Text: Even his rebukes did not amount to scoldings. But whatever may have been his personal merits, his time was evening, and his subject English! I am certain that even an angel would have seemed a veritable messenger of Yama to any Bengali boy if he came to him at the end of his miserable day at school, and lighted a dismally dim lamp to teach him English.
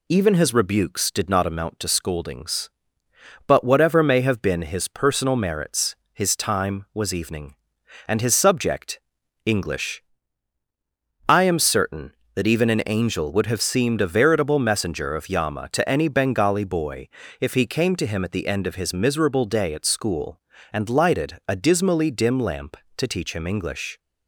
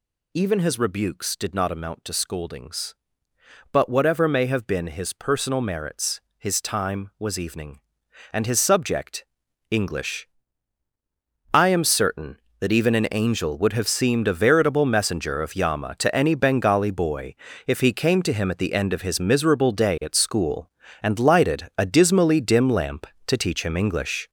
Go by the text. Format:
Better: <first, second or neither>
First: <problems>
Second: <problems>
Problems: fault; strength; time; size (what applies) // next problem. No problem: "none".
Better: first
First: pauses between "subject" and "English"; noticeable; at 8.9 s; 0.46 s long // pauses between "boy" and "if"; slight; at 17.0 s; 0.32 s long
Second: gets louder; strong; throughout; 7 dB // pauses between "subject" and "English"; noticeable; at 9.2 s; 0.46 s long // pauses between "boy" and "if"; slight; at 17.3 s; 0.32 s long